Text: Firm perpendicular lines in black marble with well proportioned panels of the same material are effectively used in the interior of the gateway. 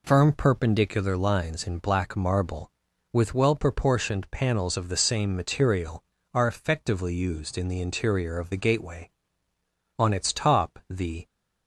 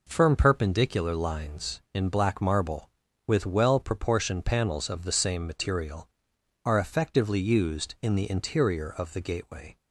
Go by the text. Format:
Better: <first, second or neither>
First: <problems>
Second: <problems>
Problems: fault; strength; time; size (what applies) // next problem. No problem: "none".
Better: second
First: goes on to say "On its top the"; noticeable; from 9.9 s on; 1.2 s long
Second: none